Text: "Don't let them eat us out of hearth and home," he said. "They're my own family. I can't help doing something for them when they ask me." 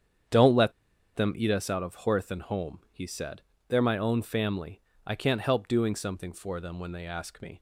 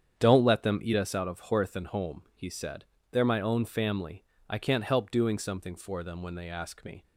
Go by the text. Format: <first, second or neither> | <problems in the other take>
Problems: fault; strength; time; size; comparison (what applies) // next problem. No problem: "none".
second | starts louder than the rest; strong; until 1.7 s; 8.5 dB; strong in the second // pauses between "let" and "them"; at 0.7 s; 0.43 s long